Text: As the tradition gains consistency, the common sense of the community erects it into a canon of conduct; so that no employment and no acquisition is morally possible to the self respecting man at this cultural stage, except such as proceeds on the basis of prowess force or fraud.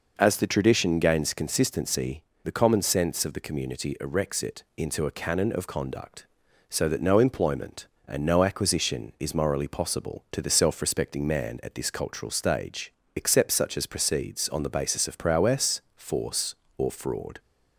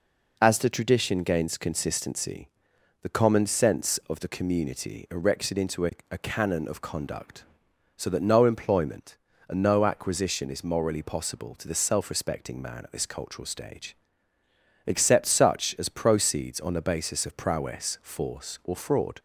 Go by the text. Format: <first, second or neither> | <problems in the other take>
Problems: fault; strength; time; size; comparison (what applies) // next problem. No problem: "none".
first | says "a" twice; at 6.1 s